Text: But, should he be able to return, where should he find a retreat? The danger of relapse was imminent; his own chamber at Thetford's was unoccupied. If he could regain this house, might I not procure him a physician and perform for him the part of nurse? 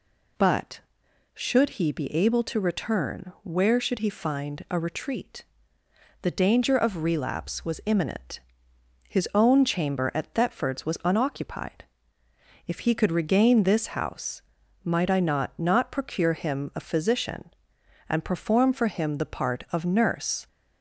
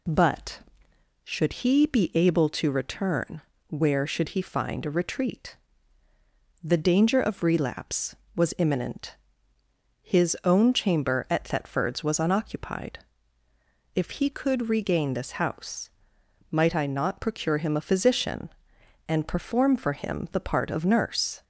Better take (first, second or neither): second